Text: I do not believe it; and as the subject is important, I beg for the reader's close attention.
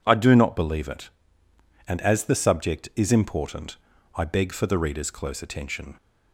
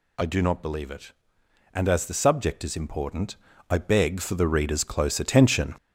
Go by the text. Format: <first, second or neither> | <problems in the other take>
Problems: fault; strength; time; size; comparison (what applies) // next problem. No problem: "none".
first | gets louder; noticeable; throughout; 6 dB